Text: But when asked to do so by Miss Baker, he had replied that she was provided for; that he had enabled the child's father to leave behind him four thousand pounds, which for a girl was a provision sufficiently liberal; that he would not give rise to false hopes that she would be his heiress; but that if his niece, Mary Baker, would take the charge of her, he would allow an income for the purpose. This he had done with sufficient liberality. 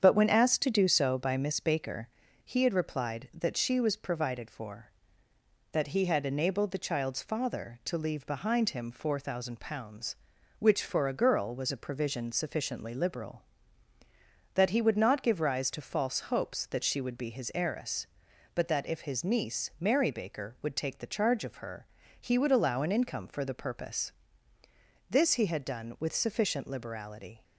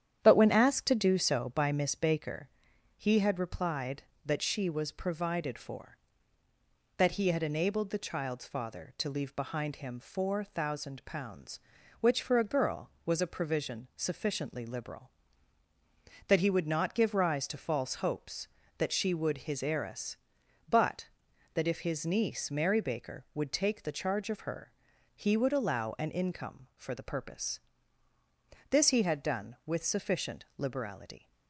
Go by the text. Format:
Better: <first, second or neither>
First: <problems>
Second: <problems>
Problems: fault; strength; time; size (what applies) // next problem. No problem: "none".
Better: first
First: starts louder than the rest; strong; until 1.0 s; 7.5 dB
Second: starts louder than the rest; strong; until 1.2 s; 9.5 dB // skips "be"; at 19.3 s